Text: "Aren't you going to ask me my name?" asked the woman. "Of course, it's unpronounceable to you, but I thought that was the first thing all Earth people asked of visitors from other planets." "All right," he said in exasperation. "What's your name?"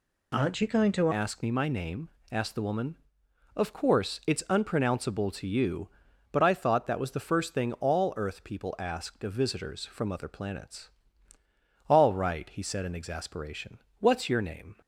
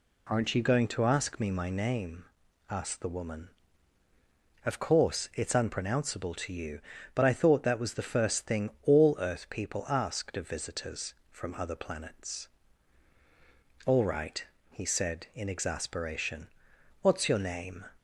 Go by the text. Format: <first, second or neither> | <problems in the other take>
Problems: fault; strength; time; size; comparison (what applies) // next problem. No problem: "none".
second | changes voice at "ask"; from 1.1 s on; 13.6 s long